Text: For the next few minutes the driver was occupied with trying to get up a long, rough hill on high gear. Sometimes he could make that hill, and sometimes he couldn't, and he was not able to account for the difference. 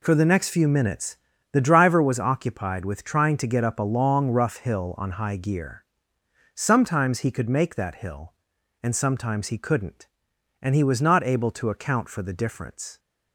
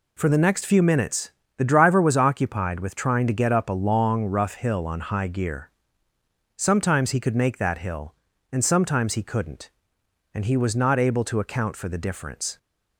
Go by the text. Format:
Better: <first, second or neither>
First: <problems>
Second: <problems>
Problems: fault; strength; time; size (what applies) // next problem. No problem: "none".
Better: neither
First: pauses between "minutes" and "the"; at 1.1 s; 0.38 s long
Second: pauses between "minutes" and "the"; slight; at 1.2 s; 0.28 s long